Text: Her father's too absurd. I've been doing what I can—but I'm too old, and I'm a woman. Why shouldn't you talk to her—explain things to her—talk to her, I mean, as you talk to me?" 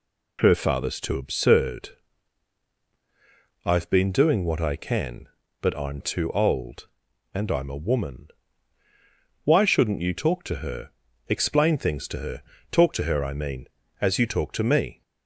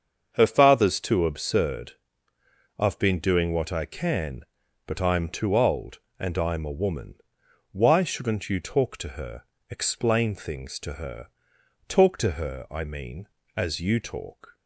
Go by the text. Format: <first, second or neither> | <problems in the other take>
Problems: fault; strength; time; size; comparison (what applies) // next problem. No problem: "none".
first | starts louder than the rest; until 1.3 s; 7 dB // stops before "to me"; at 14.5 s